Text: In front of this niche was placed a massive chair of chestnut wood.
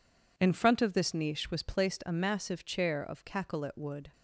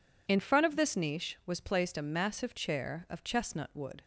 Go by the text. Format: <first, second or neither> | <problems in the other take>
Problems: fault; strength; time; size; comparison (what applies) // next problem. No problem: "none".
second | says "cacolet" for "chestnut"; at 3.2 s